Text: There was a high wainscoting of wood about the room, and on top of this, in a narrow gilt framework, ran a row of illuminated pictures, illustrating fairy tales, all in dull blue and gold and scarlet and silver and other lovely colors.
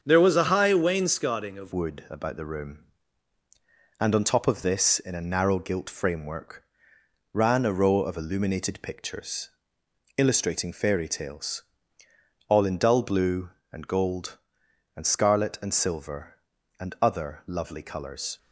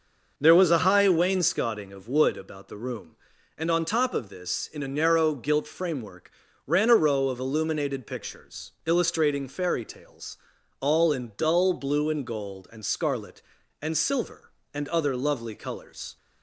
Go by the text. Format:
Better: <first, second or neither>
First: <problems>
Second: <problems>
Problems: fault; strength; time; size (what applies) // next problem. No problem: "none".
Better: second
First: starts louder than the rest; until 1.0 s; 7 dB // changes voice at "wood"; from 1.7 s on; 16.6 s long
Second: none